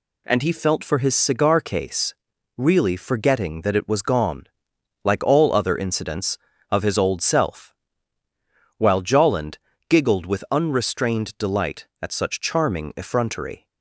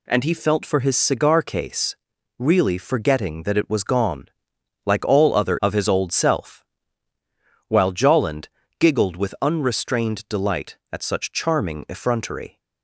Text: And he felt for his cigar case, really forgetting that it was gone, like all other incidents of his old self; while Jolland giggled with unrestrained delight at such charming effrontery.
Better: first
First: pauses between "Jolland" and "giggled"; slight; at 9.5 s; 0.28 s long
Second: skips "incidents"; at 5.6 s // pauses between "Jolland" and "giggled"; slight; at 8.4 s; 0.28 s long

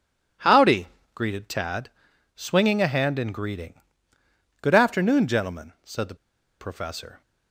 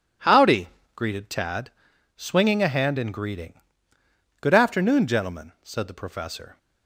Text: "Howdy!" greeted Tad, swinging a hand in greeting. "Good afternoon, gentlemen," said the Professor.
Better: second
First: pauses between "the" and "Professor"; at 6.1 s; 0.45 s long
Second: none

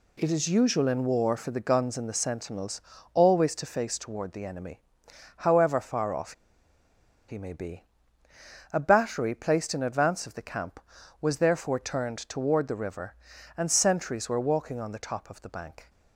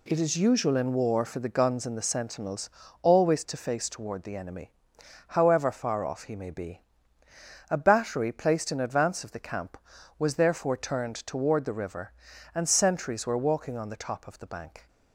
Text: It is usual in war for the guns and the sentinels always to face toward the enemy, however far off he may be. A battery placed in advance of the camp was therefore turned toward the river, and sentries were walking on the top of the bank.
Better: second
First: pauses between "sentinels" and "always"; slight; at 2.8 s; 0.32 s long // pauses between "off" and "he"; noticeable; at 6.3 s; 0.95 s long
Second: pauses between "sentinels" and "always"; slight; at 2.6 s; 0.32 s long

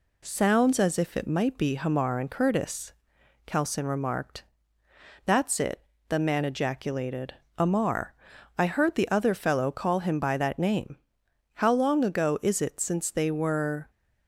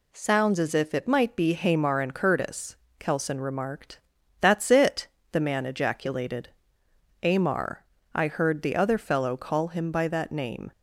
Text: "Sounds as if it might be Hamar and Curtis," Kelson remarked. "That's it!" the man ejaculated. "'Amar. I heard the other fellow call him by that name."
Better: second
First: goes on to say "How long ago is it since they were"; strong; from 11.5 s on; 2.3 s long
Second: none

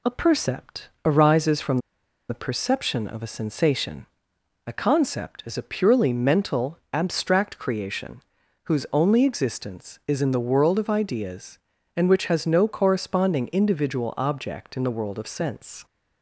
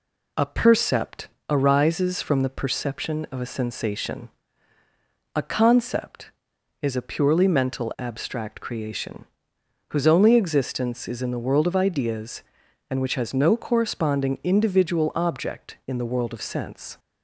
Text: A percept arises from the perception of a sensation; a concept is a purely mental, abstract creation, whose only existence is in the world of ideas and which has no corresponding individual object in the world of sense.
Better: second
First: pauses between "percept" and "arises"; slight; at 0.8 s; 0.16 s long // pauses between "from" and "the"; noticeable; at 1.7 s; 0.51 s long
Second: pauses between "percept" and "arises"; slight; at 1.2 s; 0.20 s long

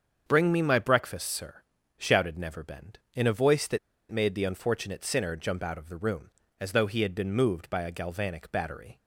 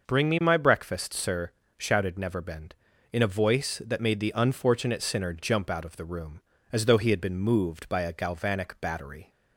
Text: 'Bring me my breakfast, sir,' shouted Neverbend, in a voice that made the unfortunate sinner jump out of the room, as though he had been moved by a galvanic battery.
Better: second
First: starts louder than the rest; until 1.2 s; 7 dB // pauses between "that" and "made"; slight; at 3.7 s; 0.32 s long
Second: none

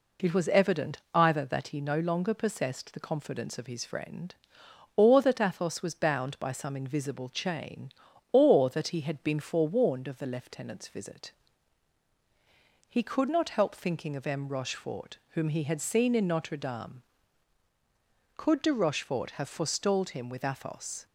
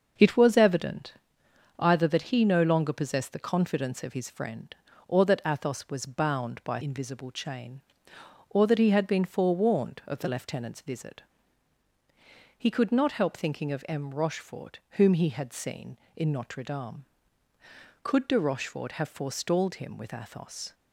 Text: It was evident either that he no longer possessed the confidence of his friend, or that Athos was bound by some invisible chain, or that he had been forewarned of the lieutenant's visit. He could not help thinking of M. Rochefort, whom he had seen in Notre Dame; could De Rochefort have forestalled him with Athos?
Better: first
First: pauses between "evident" and "either"; slight; at 0.9 s; 0.16 s long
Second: starts louder than the rest; until 1.8 s; 6 dB // pauses between "evident" and "either"; noticeable; at 1.1 s; 0.64 s long // skips "some"; at 6.8 s

